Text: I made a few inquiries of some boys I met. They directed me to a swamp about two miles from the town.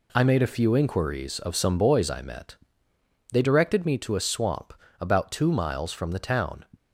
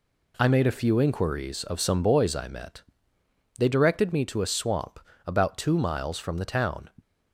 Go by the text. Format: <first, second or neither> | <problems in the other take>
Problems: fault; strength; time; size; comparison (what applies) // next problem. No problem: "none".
neither | pauses between "swamp" and "about"; slight; the same in both